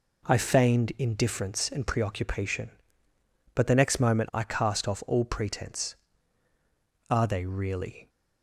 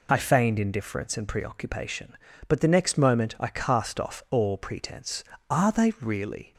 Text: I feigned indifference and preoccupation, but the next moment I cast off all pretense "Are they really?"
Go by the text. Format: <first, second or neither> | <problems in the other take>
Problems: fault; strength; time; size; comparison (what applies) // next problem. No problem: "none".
neither | none